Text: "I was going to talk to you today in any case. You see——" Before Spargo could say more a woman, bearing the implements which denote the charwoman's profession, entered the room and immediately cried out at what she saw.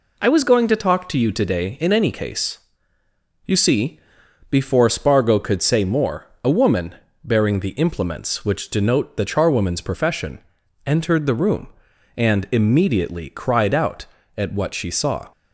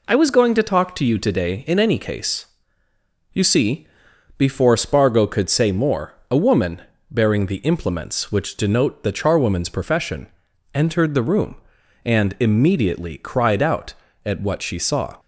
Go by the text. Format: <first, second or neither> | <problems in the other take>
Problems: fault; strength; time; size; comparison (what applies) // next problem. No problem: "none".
neither | pauses between "more" and "a"; slight; the same in both